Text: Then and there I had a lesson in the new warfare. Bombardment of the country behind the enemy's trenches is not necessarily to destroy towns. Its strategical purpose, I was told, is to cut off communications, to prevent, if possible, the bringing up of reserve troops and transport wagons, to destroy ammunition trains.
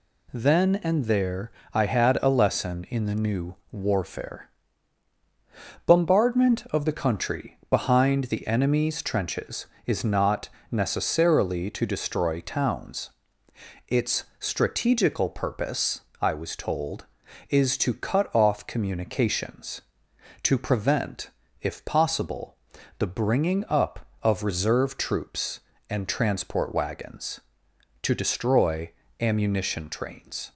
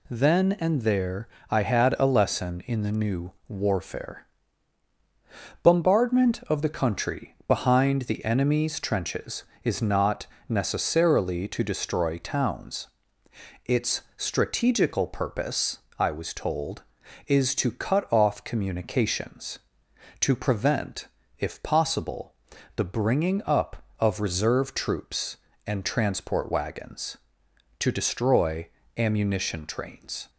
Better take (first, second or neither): neither